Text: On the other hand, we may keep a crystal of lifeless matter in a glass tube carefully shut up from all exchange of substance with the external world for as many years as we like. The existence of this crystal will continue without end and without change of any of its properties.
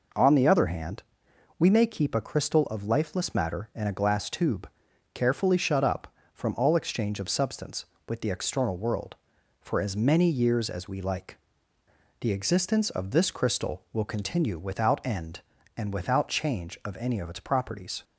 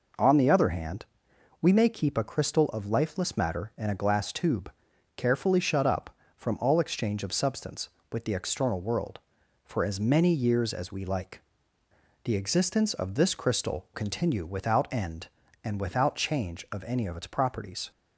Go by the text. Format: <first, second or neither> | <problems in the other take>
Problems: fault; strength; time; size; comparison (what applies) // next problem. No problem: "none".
first | pauses between "tube" and "carefully"; noticeable; at 4.7 s; 0.46 s long; noticeable in the first // skips "will"; at 13.9 s